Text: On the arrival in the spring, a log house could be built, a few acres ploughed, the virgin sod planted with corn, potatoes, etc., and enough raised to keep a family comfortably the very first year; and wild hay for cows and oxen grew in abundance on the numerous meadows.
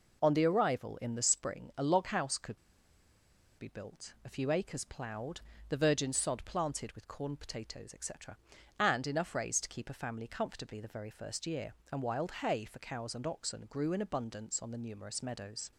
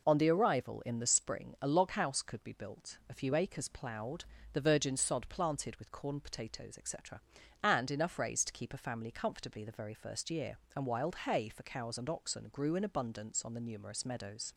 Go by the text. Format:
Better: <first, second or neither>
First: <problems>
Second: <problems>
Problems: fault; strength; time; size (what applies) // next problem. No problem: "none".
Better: second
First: pauses between "could" and "be"; at 2.5 s; 1.0 s long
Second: none